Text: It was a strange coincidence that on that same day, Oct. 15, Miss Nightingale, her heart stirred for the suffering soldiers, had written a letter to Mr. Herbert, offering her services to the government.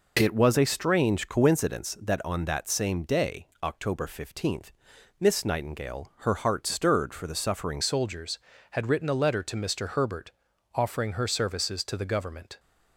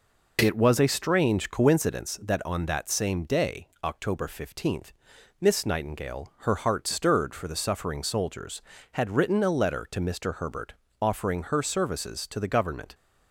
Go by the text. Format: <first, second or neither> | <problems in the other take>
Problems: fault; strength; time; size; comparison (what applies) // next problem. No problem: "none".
second | changes voice at "soldiers"; from 7.8 s on; 4.7 s long